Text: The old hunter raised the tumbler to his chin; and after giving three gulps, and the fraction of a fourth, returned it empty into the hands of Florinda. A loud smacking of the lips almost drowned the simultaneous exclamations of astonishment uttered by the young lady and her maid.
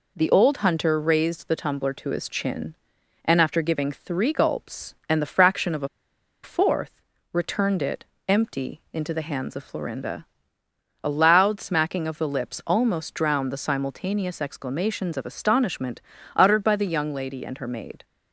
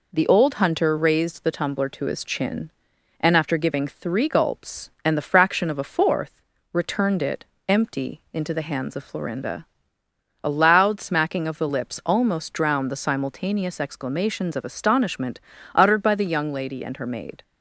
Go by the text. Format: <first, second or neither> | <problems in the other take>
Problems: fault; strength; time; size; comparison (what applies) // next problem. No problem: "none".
second | pauses between "a" and "fourth"; noticeable; at 5.8 s; 0.55 s long // pauses between "it" and "empty"; slight; at 8.0 s; 0.24 s long; slight in the second // pauses between "astonishment" and "uttered"; slight; at 16.0 s; 0.34 s long; slight in the second